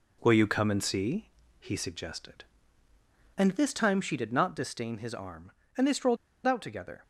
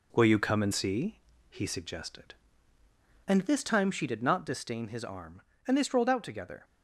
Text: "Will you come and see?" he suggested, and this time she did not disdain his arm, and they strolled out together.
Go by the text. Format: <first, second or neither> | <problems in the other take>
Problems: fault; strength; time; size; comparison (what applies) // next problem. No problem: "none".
second | pauses between "strolled" and "out"; slight; at 6.1 s; 0.29 s long